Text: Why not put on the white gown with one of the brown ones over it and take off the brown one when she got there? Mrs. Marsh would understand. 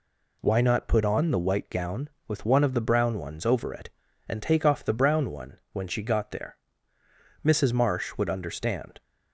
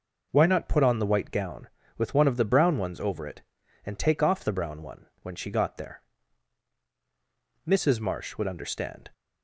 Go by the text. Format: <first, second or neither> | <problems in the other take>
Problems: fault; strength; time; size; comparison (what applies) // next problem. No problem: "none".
neither | pauses between "one" and "when"; slight; the same in both